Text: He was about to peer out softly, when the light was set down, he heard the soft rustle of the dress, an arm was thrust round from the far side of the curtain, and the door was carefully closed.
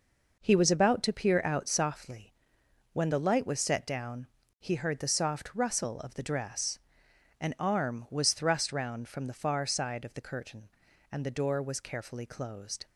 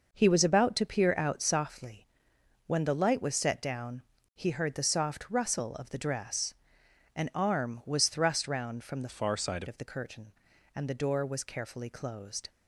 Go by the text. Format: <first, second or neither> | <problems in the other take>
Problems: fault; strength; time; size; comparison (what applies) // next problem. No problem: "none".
first | changes voice from "far" to "side"; from 9.0 to 9.6 s; 0.6 s long